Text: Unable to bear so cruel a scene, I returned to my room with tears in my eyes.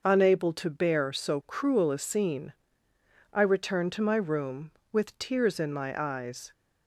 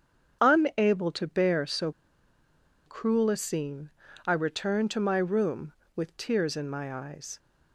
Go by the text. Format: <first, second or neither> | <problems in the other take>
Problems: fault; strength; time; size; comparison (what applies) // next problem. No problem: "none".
first | starts louder than the rest; strong; until 1.4 s; 7.5 dB // pauses between "so" and "cruel"; noticeable; at 1.9 s; 0.93 s long